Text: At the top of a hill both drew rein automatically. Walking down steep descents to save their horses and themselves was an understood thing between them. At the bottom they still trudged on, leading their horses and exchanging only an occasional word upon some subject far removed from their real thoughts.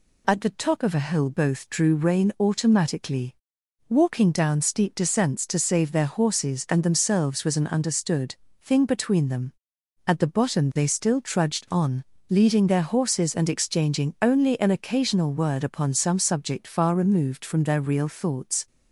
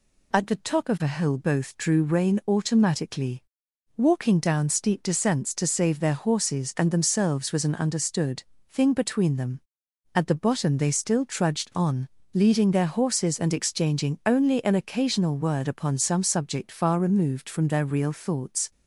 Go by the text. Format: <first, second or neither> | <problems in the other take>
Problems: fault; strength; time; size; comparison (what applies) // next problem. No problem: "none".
neither | pauses between "understood" and "thing"; slight; the same in both